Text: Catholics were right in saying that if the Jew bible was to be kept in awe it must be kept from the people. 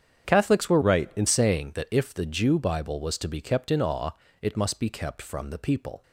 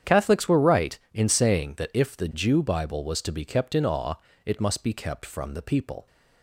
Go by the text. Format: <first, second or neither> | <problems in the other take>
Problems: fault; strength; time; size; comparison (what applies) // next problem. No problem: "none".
second | starts louder than the rest; strong; until 1.3 s; 8 dB; strong in the second // changes voice from "right" to "in"; from 0.8 to 1.2 s; 0.4 s long // pauses between "awe" and "it"; slight; at 4.1 s; 0.32 s long; slight in the second